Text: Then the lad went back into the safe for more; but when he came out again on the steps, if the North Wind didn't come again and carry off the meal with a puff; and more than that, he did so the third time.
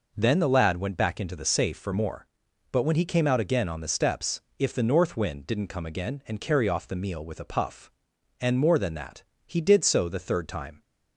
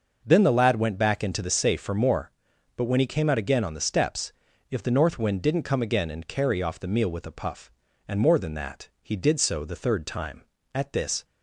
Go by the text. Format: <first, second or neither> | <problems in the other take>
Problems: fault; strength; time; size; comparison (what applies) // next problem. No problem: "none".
first | goes on to say "At this"; from 10.7 s on; 0.50 s long